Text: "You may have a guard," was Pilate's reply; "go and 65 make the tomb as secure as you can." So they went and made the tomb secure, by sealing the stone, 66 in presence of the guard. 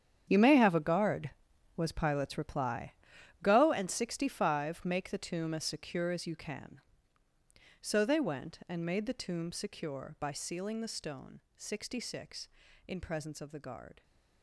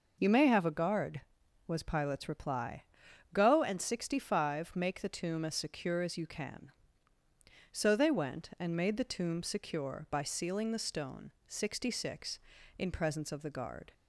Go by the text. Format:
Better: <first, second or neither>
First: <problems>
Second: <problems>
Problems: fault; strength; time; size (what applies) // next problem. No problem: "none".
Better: second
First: gets quieter; strong; throughout; 13.5 dB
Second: none